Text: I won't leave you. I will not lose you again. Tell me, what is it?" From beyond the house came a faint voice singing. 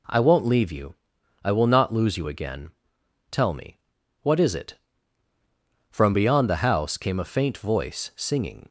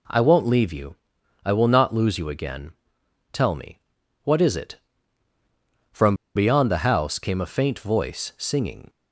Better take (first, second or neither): first